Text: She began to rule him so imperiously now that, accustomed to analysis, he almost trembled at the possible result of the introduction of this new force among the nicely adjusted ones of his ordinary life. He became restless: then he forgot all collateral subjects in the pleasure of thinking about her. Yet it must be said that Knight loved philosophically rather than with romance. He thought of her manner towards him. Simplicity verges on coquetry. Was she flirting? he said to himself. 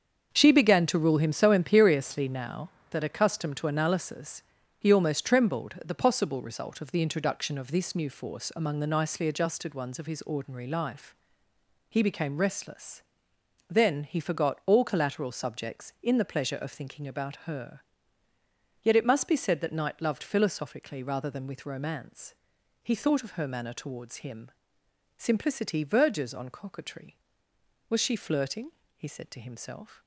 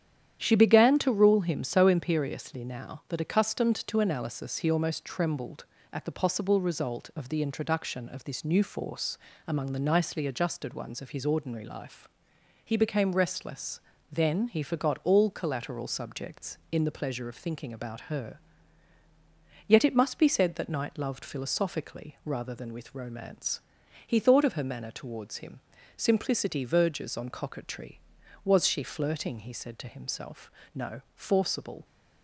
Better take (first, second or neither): first